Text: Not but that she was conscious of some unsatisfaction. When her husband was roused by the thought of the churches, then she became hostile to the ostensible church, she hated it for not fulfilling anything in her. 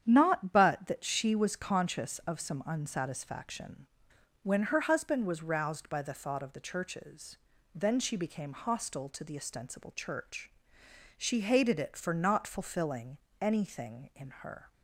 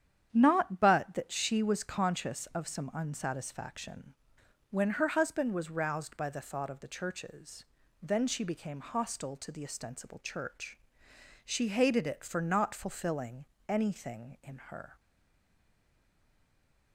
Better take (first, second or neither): first